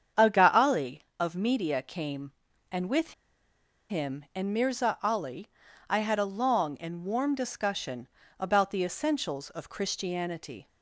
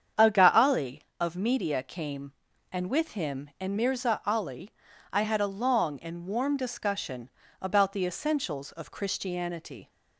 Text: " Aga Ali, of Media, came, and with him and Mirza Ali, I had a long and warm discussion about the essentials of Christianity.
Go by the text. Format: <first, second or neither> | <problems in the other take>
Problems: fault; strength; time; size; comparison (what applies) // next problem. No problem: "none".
second | starts louder than the rest; strong; until 1.3 s; 8 dB; strong in the second // pauses between "with" and "him"; noticeable; at 3.1 s; 0.76 s long // pauses between "discussion" and "about"; slight; at 8.0 s; 0.32 s long; slight in the second